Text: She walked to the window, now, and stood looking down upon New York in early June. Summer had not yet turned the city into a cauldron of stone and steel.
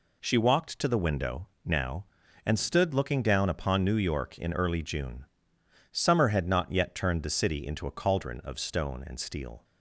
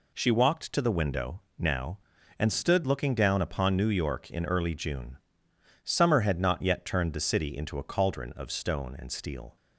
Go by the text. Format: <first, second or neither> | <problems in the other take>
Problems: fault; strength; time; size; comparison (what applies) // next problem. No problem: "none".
neither | none